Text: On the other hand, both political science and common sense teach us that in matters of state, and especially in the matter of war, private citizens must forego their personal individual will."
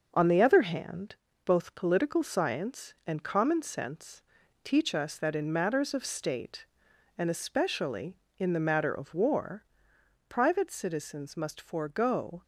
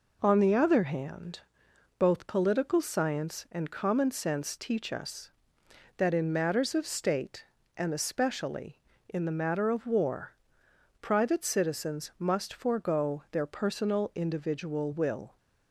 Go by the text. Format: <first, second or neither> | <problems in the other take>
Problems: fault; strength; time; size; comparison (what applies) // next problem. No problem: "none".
second | starts louder than the rest; until 1.1 s; 6 dB // pauses between "sense" and "teach"; at 4.2 s; 0.42 s long // stops before "their personal individual will"; at 12.4 s